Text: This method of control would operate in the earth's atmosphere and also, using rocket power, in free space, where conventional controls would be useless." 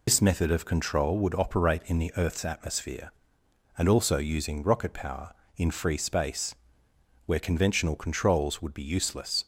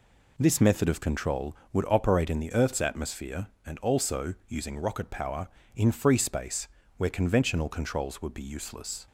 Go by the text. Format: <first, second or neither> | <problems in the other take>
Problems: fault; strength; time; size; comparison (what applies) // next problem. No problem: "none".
second | loses the start of "This"; at 0.0 s; 85 ms